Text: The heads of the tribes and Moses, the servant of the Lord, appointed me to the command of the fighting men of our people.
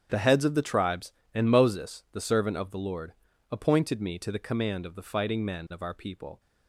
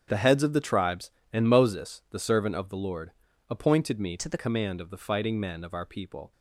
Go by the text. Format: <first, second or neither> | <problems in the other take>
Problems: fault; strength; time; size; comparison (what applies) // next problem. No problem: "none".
first | starts louder than the rest; strong; until 1.0 s; 7.5 dB; strong in the first // changes voice from "to" to "the"; from 4.1 to 4.3 s; 0.2 s long